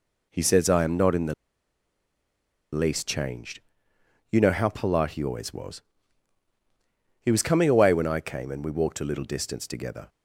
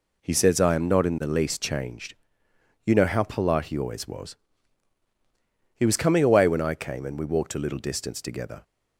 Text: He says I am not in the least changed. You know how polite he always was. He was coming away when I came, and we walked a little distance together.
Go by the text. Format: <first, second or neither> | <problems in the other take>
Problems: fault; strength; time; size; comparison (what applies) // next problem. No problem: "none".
second | pauses between "the" and "least"; strong; at 1.3 s; 1.3 s long